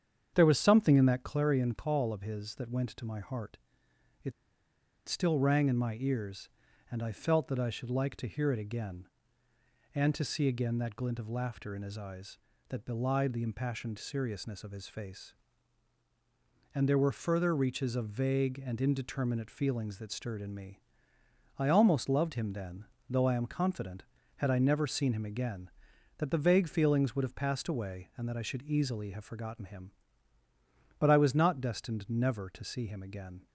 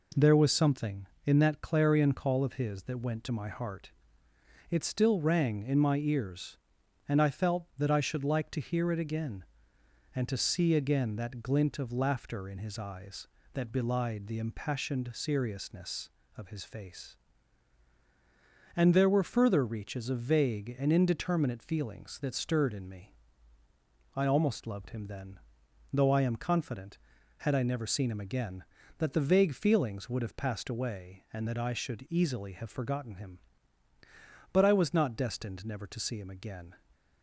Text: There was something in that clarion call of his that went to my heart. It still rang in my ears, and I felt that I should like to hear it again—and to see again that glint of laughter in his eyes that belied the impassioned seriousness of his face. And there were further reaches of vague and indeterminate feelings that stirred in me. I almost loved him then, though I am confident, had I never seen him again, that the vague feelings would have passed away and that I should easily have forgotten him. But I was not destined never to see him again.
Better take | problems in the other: second | starts louder than the rest; strong; until 1.3 s; 8 dB // pauses between "It" and "still"; noticeable; at 4.3 s; 0.74 s long

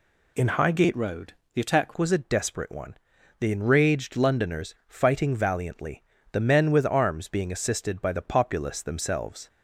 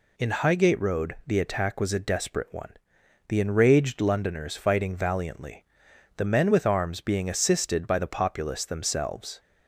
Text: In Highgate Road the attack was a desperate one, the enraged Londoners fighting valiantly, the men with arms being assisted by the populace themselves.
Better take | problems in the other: second | changes voice from "Road" to "attack"; from 0.9 to 1.9 s; 1.0 s long // pauses between "Road" and "the"; slight; at 1.3 s; 0.20 s long

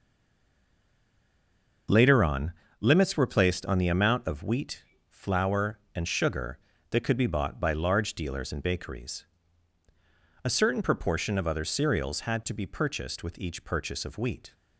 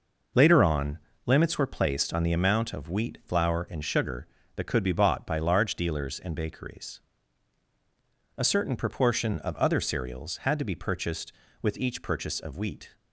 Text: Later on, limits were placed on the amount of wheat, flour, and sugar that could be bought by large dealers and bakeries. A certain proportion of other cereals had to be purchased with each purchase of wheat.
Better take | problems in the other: second | stays silent before the first word; noticeable; until 1.8 s; 1.8 s long

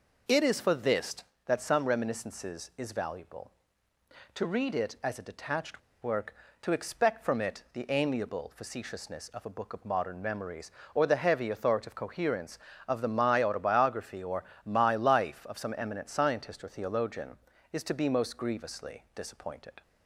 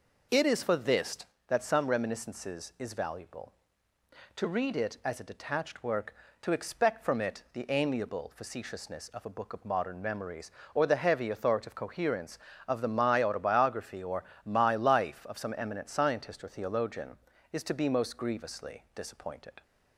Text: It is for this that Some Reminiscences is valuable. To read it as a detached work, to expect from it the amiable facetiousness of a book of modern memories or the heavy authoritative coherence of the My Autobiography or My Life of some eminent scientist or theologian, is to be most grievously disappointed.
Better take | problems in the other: second | pauses between "detached" and "work"; slight; at 5.8 s; 0.21 s long // pauses between "or" and "My"; slight; at 14.4 s; 0.18 s long; slight in the second

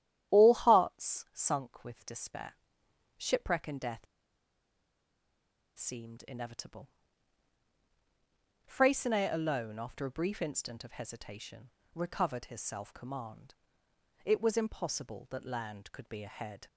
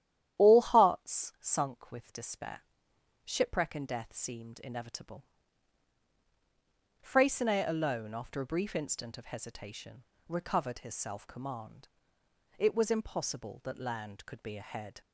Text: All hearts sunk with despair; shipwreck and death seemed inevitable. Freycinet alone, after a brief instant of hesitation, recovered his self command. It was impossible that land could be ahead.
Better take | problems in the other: second | starts louder than the rest; strong; until 1.4 s; 11 dB; strong in the second // pauses between "death" and "seemed"; strong; at 4.0 s; 1.7 s long

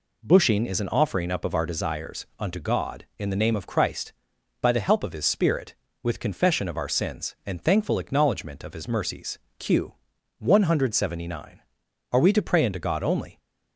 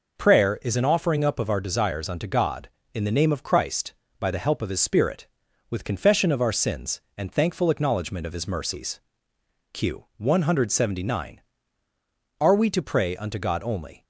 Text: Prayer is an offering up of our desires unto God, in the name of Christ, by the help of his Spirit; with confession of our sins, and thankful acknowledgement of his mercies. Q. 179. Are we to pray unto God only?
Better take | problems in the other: second | says "Bushing" for "Prayer"; at 0.2 s

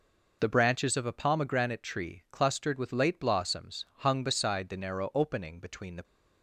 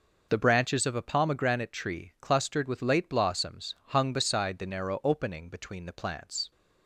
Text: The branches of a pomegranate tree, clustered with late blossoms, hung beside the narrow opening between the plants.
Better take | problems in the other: second | stops before "plants"; at 6.0 s

